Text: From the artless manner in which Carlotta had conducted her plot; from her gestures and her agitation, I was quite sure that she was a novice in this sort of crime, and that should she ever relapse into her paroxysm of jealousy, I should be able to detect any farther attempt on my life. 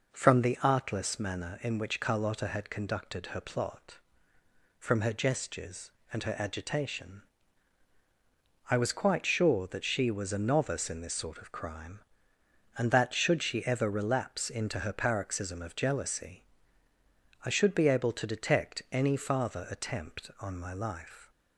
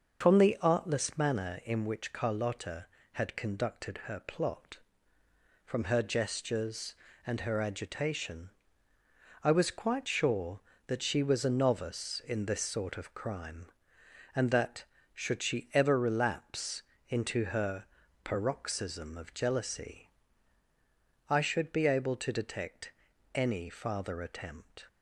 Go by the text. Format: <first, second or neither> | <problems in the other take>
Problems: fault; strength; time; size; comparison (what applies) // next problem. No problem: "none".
first | starts louder than the rest; until 1.2 s; 6.5 dB // pauses between "relapse" and "into"; slight; at 16.8 s; 0.24 s long // pauses between "her" and "paroxysm"; at 17.8 s; 0.38 s long // pauses between "detect" and "any"; at 22.9 s; 0.42 s long // stops before "on my life"; at 24.8 s